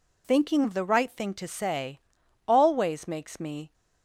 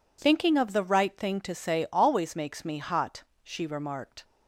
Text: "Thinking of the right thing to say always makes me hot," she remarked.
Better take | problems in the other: second | pauses between "say" and "always"; noticeable; at 1.9 s; 0.48 s long // stops before "hot she remarked"; at 3.7 s

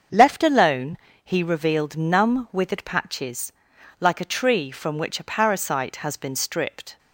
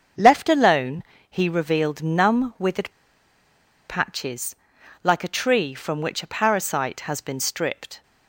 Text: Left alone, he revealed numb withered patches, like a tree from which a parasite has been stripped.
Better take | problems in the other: first | starts louder than the rest; until 1.4 s; 7 dB; also in the first // pauses between "withered" and "patches"; noticeable; at 2.9 s; 0.97 s long

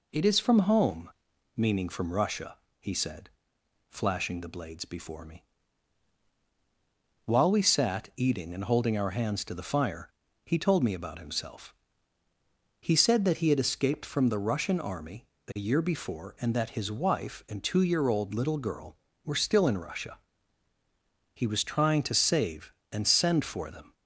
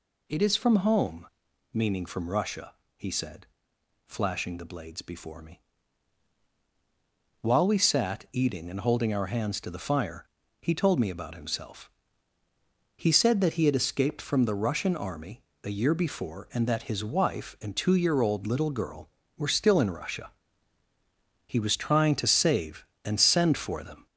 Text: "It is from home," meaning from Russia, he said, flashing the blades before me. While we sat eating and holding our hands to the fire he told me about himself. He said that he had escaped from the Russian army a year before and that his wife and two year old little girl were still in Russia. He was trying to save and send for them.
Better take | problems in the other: first | gets louder; noticeable; throughout; 4 dB // pauses between "fire" and "he"; slight; at 10.2 s; 0.34 s long; slight in the first // pauses between "army" and "a"; slight; at 15.4 s; 0.22 s long; slight in the first

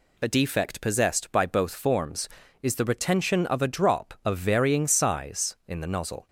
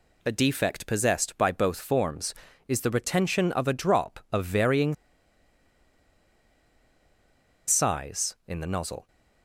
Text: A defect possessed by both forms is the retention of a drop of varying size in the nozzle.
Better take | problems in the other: first | pauses between "varying" and "size"; strong; at 4.9 s; 2.7 s long

